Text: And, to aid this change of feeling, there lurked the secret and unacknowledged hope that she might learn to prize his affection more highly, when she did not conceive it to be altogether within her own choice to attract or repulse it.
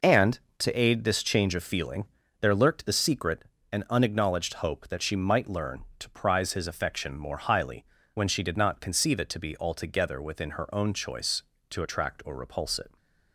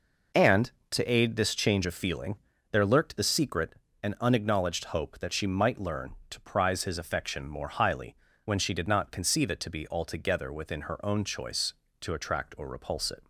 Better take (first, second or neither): neither